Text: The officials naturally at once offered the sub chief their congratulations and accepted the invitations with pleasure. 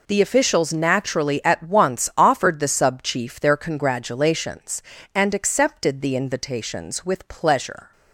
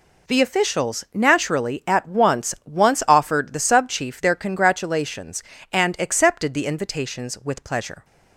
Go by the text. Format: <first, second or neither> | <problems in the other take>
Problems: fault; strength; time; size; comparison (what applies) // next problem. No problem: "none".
first | says "once" twice; at 2.6 s